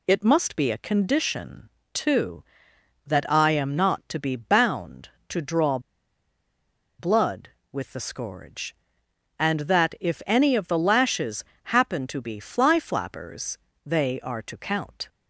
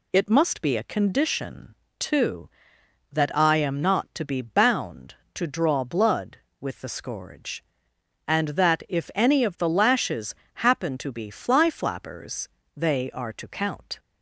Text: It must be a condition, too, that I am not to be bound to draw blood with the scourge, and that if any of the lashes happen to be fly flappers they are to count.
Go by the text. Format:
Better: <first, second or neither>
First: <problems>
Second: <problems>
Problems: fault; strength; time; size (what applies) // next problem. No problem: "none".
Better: second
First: pauses between "draw" and "blood"; at 5.7 s; 1.2 s long // pauses between "lashes" and "happen"; slight; at 11.4 s; 0.20 s long // pauses between "flappers" and "they"; slight; at 13.5 s; 0.28 s long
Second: pauses between "lashes" and "happen"; slight; at 10.3 s; 0.20 s long // pauses between "flappers" and "they"; slight; at 12.4 s; 0.28 s long